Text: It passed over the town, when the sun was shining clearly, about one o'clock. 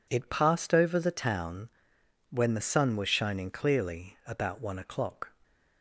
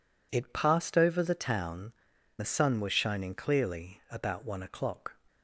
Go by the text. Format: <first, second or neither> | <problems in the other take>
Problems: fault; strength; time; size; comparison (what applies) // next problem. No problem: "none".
first | skips "when"; at 2.1 s